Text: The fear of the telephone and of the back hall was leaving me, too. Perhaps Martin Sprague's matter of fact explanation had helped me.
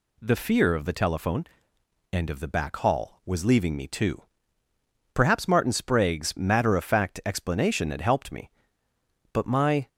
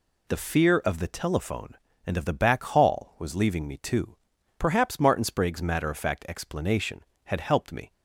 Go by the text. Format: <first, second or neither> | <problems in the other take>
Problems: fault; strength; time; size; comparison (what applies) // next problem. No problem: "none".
second | goes on to say "But my"; from 9.3 s on; 0.56 s long